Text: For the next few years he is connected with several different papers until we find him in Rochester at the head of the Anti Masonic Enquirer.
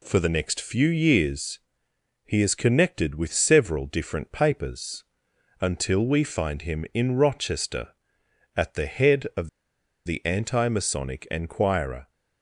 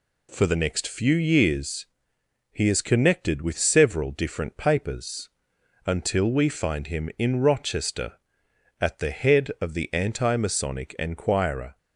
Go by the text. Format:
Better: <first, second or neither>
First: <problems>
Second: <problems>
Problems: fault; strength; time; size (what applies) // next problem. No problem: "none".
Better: second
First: pauses between "years" and "he"; noticeable; at 1.5 s; 0.66 s long // pauses between "papers" and "until"; noticeable; at 5.0 s; 0.58 s long // pauses between "of" and "the"; noticeable; at 9.4 s; 0.56 s long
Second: pauses between "years" and "he"; noticeable; at 1.8 s; 0.66 s long // pauses between "papers" and "until"; noticeable; at 5.2 s; 0.58 s long